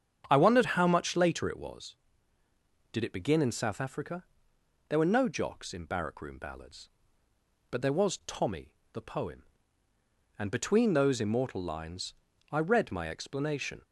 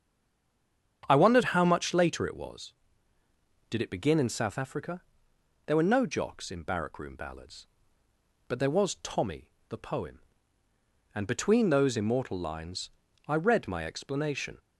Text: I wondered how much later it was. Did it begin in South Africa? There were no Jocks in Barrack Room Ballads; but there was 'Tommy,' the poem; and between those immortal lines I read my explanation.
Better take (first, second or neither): first